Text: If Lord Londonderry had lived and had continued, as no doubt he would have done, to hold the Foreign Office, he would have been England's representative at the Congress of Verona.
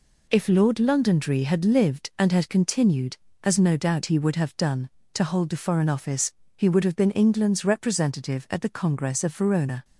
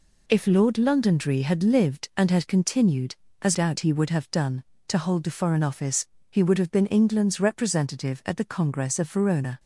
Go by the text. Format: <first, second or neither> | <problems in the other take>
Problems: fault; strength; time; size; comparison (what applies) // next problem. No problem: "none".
first | skips "no"; at 3.5 s